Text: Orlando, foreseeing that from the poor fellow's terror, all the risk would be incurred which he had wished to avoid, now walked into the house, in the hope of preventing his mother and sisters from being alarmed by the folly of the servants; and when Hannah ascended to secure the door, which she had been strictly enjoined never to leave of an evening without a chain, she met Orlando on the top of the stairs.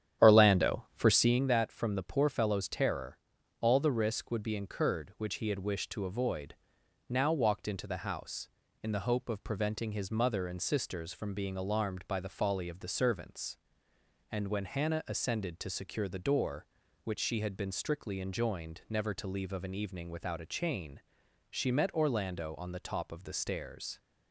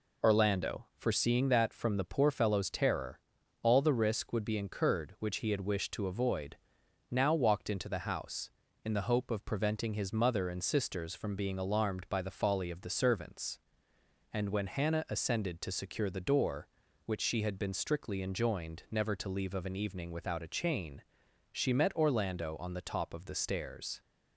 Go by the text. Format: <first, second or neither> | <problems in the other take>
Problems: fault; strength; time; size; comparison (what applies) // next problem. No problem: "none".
second | starts louder than the rest; strong; until 1.4 s; 10 dB